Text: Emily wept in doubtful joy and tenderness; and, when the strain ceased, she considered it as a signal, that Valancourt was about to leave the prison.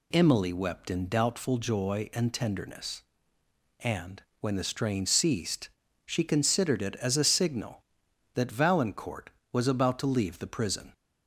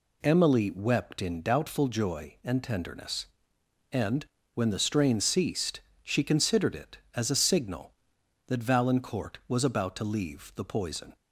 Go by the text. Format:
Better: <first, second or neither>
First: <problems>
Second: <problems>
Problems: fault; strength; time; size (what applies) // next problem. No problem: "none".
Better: first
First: none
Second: says "poison" for "prison"; at 10.6 s